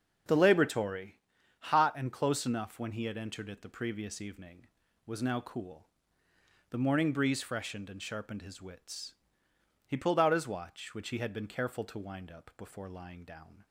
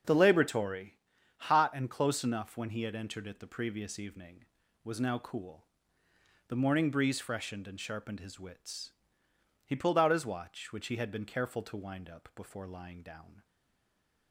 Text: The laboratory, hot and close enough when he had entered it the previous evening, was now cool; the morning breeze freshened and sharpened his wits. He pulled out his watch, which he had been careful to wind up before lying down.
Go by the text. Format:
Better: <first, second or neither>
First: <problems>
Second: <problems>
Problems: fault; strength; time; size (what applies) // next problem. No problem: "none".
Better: first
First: starts louder than the rest; until 1.6 s; 6.5 dB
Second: starts louder than the rest; until 1.4 s; 6.5 dB // stays silent after the last word; slight; from 13.4 s on; 0.9 s long